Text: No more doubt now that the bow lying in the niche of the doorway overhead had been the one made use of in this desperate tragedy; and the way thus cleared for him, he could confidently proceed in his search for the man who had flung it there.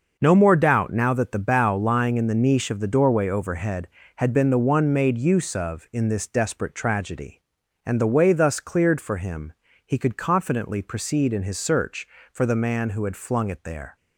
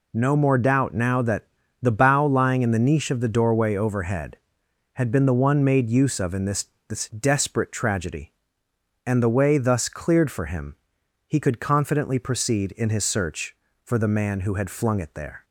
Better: first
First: none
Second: pauses between "that" and "the"; slight; at 1.4 s; 0.36 s long // says "this" twice; at 6.8 s

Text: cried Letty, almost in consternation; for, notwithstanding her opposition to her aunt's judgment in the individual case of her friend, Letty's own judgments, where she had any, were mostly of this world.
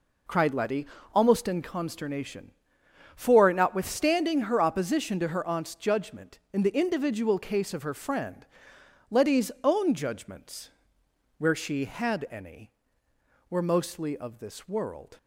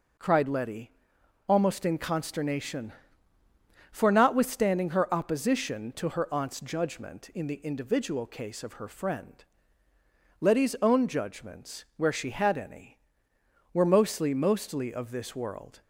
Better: first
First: none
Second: says "mostly" twice; at 14.3 s

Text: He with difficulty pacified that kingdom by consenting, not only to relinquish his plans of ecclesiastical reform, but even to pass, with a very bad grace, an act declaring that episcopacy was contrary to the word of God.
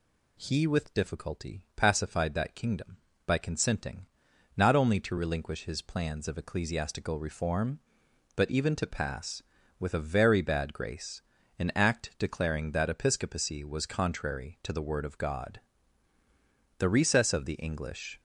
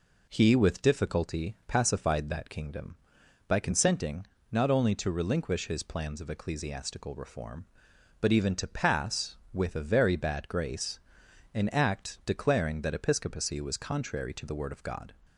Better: second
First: goes on to say "The recess of the English"; from 16.7 s on; 1.4 s long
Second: none

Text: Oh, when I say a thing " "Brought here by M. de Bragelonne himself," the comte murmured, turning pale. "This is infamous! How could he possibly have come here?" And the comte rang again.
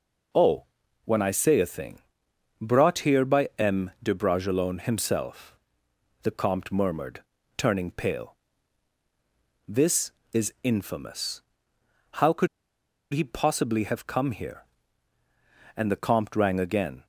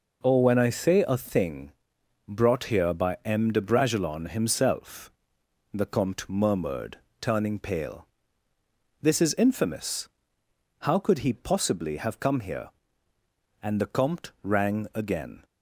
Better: second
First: pauses between "could" and "he"; noticeable; at 12.4 s; 0.65 s long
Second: none

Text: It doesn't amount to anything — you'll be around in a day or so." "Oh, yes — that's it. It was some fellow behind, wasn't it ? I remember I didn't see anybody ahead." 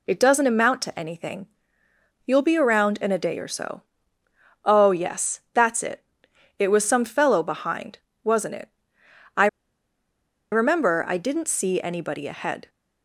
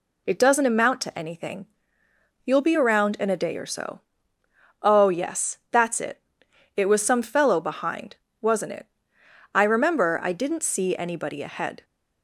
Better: second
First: pauses between "I" and "remember"; at 9.4 s; 1.0 s long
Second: none

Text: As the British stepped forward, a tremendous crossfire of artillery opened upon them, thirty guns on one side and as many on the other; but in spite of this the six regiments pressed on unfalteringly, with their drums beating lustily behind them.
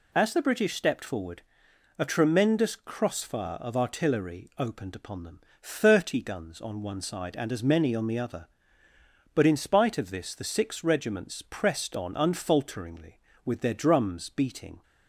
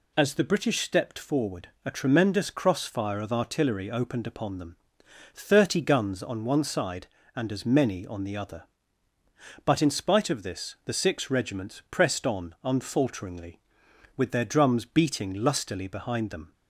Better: second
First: stops before "lustily behind them"; at 14.8 s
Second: none

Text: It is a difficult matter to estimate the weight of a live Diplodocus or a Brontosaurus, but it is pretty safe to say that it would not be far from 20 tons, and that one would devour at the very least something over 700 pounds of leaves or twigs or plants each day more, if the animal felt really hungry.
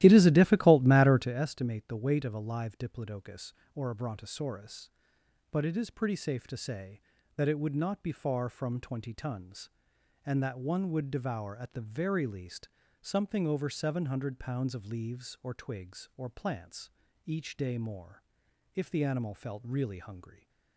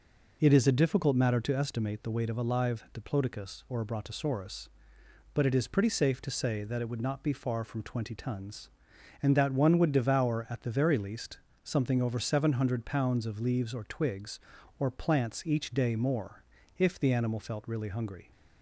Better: second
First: starts louder than the rest; strong; until 1.5 s; 14.5 dB // pauses between "least" and "something"; slight; at 12.6 s; 0.32 s long // pauses between "plants" and "each"; slight; at 16.8 s; 0.34 s long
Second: pauses between "least" and "something"; slight; at 11.3 s; 0.24 s long

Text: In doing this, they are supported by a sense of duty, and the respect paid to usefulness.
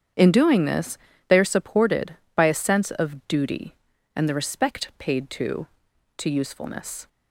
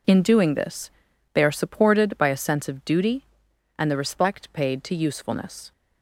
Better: second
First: starts louder than the rest; strong; until 1.4 s; 8.5 dB // says "to" twice; at 6.1 s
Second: none

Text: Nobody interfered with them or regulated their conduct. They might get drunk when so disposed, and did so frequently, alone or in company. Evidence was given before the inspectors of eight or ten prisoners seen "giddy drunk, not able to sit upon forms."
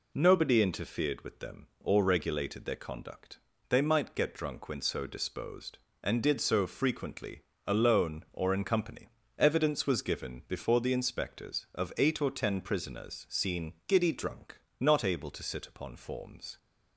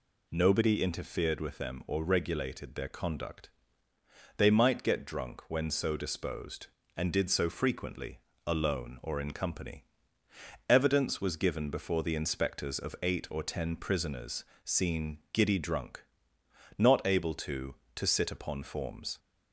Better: first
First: none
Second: pauses between "prisoners" and "seen"; slight; at 14.4 s; 0.22 s long // says "to" twice; at 17.9 s

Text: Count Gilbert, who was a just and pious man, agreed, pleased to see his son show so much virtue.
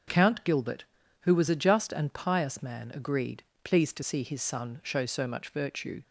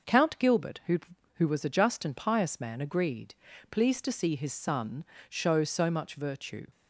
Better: first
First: none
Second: starts louder than the rest; noticeable; until 1.4 s; 6 dB // says "who" twice; at 1.3 s // pauses between "son" and "show"; slight; at 5.0 s; 0.24 s long

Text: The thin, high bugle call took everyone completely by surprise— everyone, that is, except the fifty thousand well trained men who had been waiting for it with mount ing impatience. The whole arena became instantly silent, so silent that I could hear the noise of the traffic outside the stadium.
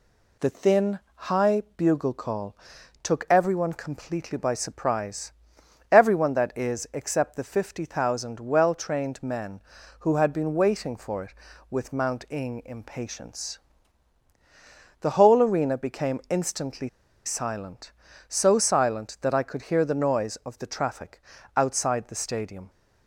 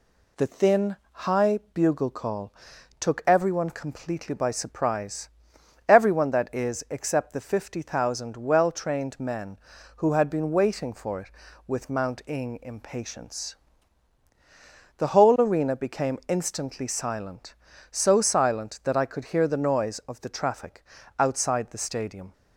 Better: second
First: pauses between "call" and "took"; noticeable; at 2.5 s; 0.46 s long // pauses between "instantly" and "silent"; at 16.8 s; 0.37 s long // pauses between "traffic" and "outside"; slight; at 21.2 s; 0.34 s long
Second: pauses between "call" and "took"; noticeable; at 2.5 s; 0.46 s long // pauses between "traffic" and "outside"; slight; at 20.8 s; 0.34 s long

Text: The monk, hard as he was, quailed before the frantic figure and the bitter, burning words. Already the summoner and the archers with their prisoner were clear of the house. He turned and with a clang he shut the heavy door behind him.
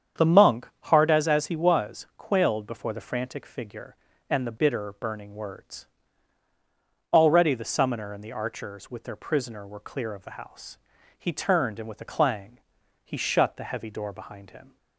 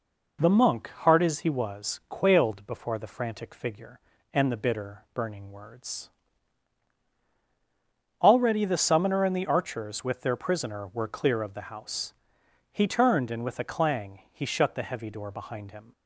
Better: second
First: starts louder than the rest; strong; until 1.3 s; 8 dB // says "as" twice; at 1.2 s // pauses between "clang" and "he"; at 12.6 s; 0.44 s long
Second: none

